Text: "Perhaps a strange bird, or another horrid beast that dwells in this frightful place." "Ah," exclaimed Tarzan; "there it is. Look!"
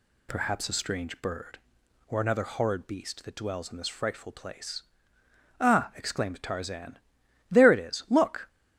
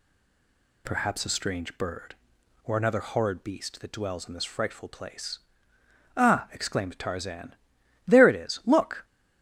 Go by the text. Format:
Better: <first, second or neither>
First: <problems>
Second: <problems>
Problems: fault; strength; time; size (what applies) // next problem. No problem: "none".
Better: first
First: none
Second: stays silent before the first word; slight; until 0.8 s; 0.8 s long